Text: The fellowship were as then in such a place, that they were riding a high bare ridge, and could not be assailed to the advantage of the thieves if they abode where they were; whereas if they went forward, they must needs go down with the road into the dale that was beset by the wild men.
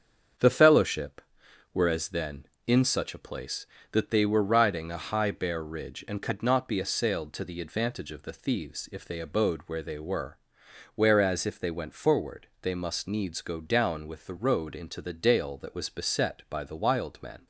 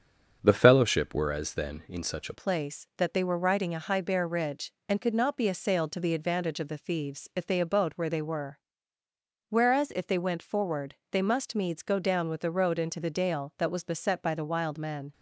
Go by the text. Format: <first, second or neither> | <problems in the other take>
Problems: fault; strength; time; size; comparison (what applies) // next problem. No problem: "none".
first | starts louder than the rest; until 1.4 s; 6.5 dB; strong in the first // changes voice at "place"; from 2.3 s on; 12.8 s long